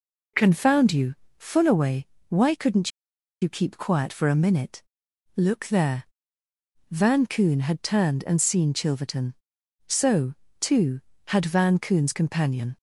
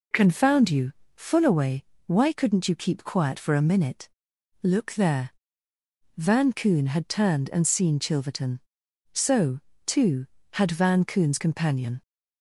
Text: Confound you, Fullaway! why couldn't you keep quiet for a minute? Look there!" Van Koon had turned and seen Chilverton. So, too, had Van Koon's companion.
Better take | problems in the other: second | pauses between "couldn't" and "you"; noticeable; at 2.8 s; 0.52 s long

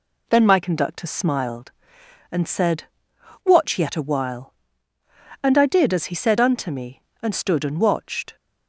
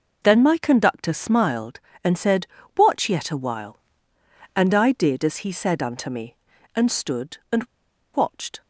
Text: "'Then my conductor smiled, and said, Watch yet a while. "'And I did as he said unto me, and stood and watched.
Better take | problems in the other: first | pauses between "and" and "watched"; noticeable; at 7.6 s; 0.49 s long

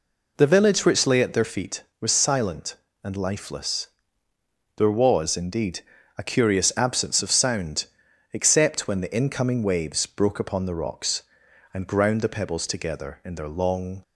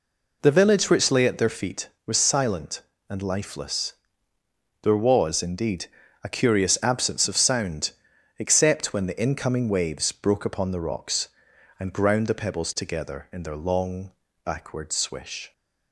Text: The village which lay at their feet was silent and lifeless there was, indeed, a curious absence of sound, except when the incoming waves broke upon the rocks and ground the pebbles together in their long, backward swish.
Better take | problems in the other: second | pauses between "lifeless" and "there"; noticeable; at 3.8 s; 0.88 s long; noticeable in the second // stops before "backward swish"; at 14.0 s

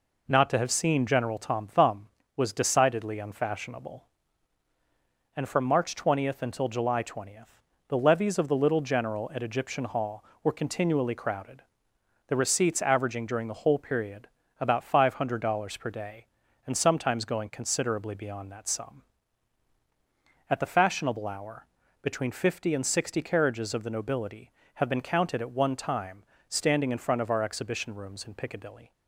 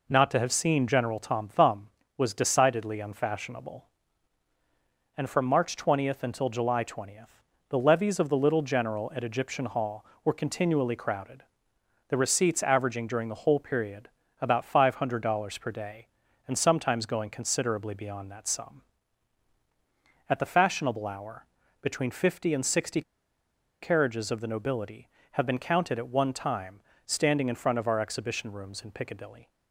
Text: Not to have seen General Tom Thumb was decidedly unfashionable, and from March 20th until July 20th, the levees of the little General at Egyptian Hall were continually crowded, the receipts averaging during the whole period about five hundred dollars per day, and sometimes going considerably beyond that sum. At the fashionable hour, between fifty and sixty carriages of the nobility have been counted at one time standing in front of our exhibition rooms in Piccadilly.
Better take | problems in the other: first | pauses between "period" and "about"; slight; at 14.0 s; 0.34 s long; slight in the first // pauses between "sixty" and "carriages"; noticeable; at 23.0 s; 0.80 s long // pauses between "time" and "standing"; slight; at 26.8 s; 0.24 s long; slight in the first

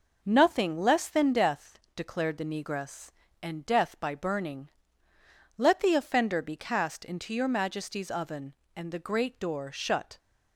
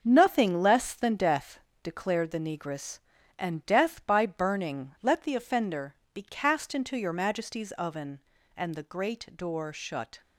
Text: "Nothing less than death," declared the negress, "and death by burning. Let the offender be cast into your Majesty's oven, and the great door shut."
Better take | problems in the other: first | gets quieter; strong; throughout; 8.5 dB // pauses between "offender" and "be"; slight; at 5.9 s; 0.20 s long

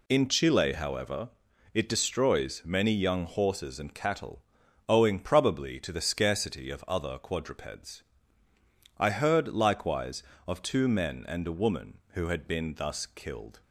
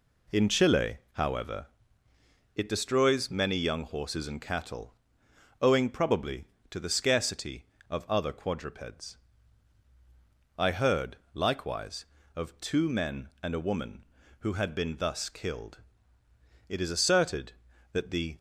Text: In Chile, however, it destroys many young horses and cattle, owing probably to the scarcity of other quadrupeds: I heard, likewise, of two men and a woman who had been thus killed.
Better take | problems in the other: first | goes on to say "It is asserted that the"; strong; from 16.6 s on; 1.6 s long

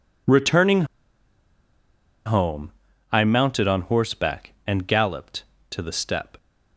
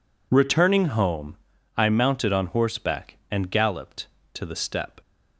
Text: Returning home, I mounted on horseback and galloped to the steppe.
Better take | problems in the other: second | pauses between "Returning" and "home"; strong; at 0.8 s; 1.4 s long

